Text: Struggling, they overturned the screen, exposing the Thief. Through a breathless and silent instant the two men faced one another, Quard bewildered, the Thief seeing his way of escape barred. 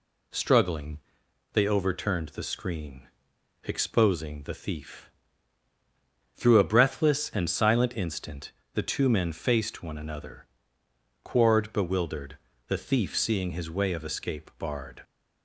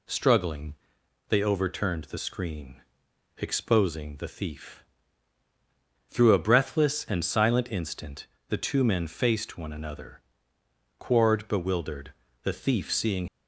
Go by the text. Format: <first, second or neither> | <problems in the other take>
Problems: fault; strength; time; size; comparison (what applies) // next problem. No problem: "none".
first | pauses between "instant" and "the"; slight; at 8.2 s; 0.22 s long; slight in the first // stops before "his way of escape barred"; at 13.2 s